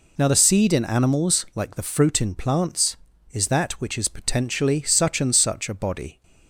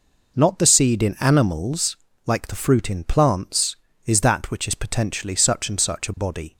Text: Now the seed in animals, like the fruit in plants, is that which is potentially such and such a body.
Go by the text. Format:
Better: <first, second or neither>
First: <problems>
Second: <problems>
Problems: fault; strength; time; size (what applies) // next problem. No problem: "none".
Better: first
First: none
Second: says "Not" for "Now"; at 0.3 s